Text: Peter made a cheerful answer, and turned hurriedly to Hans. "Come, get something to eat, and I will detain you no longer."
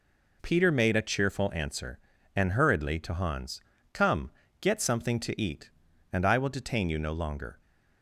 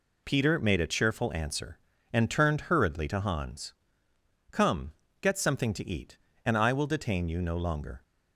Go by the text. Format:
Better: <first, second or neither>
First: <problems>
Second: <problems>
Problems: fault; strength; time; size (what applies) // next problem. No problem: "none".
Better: second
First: skips "turned"; at 2.5 s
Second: none